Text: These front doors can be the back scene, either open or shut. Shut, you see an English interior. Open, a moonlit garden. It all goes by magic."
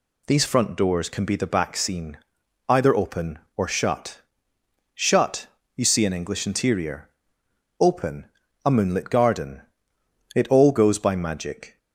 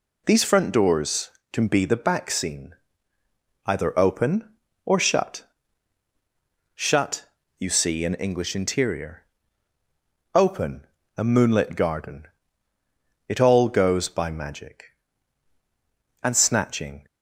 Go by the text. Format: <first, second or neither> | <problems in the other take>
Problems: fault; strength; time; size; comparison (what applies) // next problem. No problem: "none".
first | goes on to say "And snatching"; noticeable; from 16.2 s on; 0.82 s long